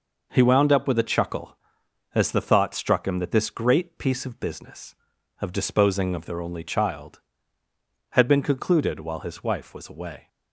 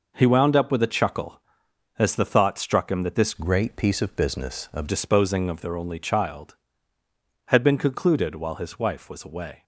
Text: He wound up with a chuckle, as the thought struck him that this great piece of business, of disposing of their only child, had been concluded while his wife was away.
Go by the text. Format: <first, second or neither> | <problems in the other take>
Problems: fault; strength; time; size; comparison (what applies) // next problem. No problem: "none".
first | changes voice from "great" to "of"; from 3.3 to 4.8 s; 1.5 s long